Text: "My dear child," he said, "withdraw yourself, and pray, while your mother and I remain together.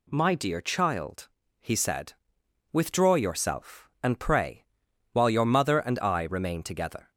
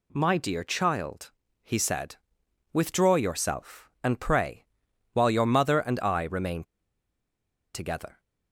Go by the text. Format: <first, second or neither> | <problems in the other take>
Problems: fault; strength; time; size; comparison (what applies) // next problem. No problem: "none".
first | pauses between "remain" and "together"; at 6.6 s; 1.0 s long